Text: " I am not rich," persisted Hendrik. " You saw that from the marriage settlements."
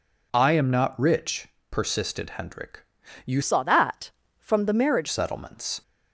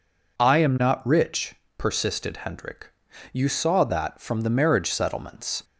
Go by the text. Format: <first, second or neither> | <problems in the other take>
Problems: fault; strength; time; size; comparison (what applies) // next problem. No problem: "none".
second | changes voice from "saw" to "marriage"; from 3.4 to 5.0 s; 1.6 s long